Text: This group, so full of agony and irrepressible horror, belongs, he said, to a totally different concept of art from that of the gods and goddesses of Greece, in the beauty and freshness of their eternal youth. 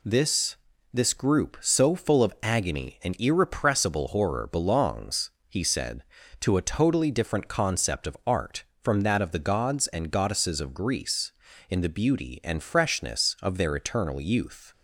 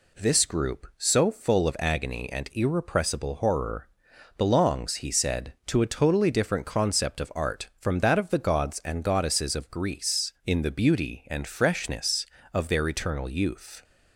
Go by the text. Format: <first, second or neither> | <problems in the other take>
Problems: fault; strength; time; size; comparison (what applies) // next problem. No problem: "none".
second | says "This" twice; at 0.9 s